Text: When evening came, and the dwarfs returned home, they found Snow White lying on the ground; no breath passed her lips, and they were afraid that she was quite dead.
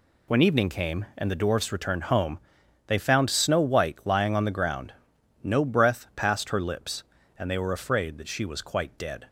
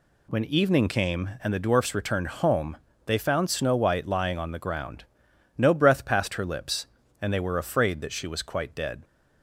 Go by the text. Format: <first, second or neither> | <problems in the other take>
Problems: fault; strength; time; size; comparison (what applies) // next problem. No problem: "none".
neither | none